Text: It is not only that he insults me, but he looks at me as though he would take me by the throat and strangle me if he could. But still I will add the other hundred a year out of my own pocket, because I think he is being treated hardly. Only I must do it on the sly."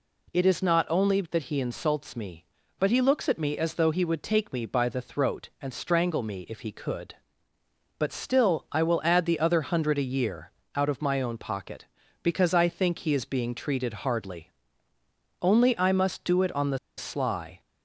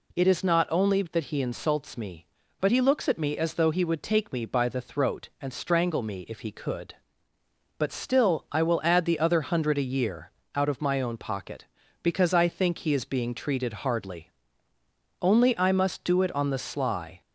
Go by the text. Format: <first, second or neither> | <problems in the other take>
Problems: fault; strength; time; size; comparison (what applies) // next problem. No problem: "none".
second | pauses between "year" and "out"; slight; at 10.5 s; 0.24 s long; slight in the second // pauses between "the" and "sly"; slight; at 16.7 s; 0.19 s long